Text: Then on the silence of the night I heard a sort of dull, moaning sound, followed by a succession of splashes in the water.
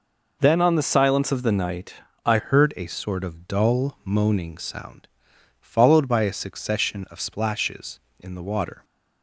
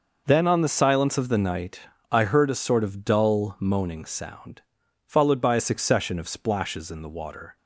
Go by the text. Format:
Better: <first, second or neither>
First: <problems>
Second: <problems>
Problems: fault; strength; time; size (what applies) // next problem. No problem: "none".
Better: second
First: pauses between "night" and "I"; slight; at 1.9 s; 0.32 s long // changes voice at "heard"; from 2.3 s on; 6.5 s long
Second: pauses between "night" and "I"; slight; at 1.8 s; 0.32 s long